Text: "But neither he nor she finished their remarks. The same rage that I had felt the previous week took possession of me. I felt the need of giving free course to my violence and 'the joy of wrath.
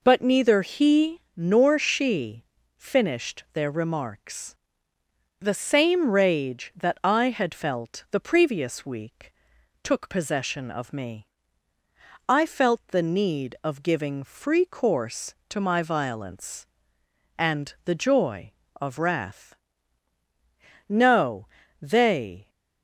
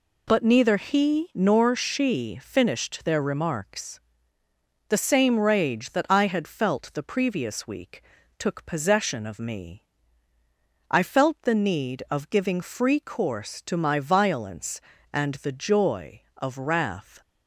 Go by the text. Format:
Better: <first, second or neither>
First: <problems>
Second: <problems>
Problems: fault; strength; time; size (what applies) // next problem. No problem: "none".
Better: second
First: pauses between "she" and "finished"; slight; at 2.4 s; 0.32 s long // pauses between "week" and "took"; noticeable; at 9.3 s; 0.48 s long // goes on to say "No they"; from 20.8 s on; 1.6 s long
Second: pauses between "week" and "took"; slight; at 8.0 s; 0.34 s long